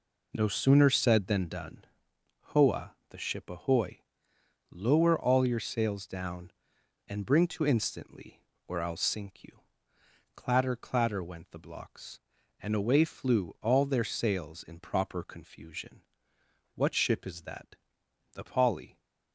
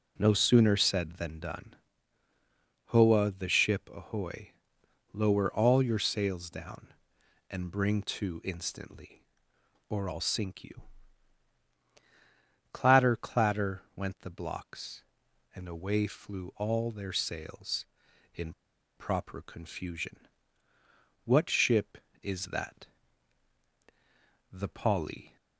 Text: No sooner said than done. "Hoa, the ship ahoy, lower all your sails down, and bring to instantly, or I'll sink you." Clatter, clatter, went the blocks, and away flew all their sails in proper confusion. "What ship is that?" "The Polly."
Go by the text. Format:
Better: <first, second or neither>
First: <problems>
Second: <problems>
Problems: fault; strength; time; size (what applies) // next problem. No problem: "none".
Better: first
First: none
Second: pauses between "in" and "proper"; at 18.5 s; 0.43 s long